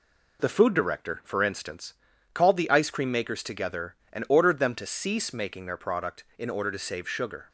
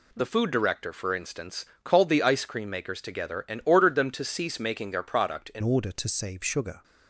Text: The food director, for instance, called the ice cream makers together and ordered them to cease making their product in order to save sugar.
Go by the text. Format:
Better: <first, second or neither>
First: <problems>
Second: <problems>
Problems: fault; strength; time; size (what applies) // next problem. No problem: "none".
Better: first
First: none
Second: changes voice at "order"; from 5.6 s on; 1.2 s long